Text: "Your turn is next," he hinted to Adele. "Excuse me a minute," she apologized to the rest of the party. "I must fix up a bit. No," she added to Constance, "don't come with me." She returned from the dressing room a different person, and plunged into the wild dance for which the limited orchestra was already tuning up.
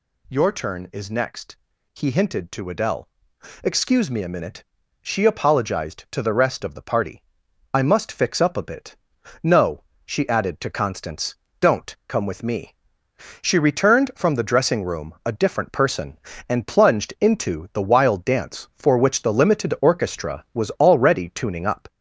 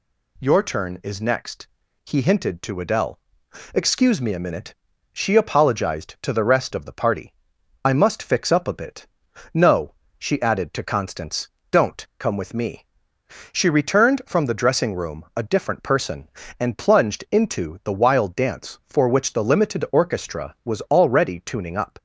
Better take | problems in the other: second | gets louder; throughout; 3.5 dB

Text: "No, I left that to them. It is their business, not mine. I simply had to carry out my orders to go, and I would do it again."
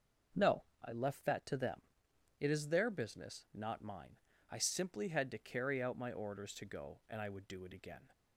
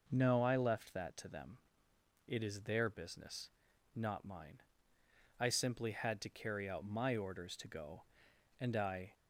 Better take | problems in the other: first | stops before "would do it again"; at 9.1 s

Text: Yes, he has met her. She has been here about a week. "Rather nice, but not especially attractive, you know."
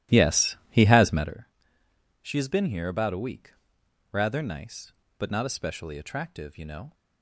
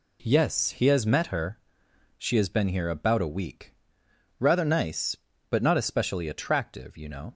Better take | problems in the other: second | starts louder than the rest; strong; until 1.4 s; 13.5 dB

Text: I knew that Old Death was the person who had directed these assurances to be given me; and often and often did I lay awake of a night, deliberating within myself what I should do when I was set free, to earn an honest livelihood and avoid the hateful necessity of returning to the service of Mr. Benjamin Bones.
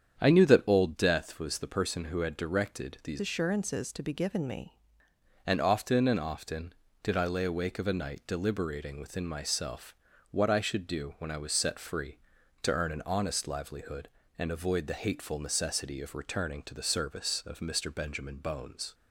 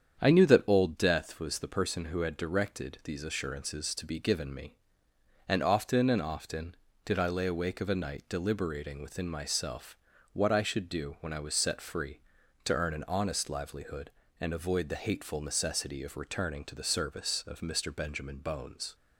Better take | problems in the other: second | starts louder than the rest; strong; until 1.2 s; 8 dB; strong in the second // changes voice from "assurances" to "me"; from 3.1 to 4.7 s; 1.6 s long // pauses between "myself" and "what"; at 9.9 s; 0.38 s long; also in the second

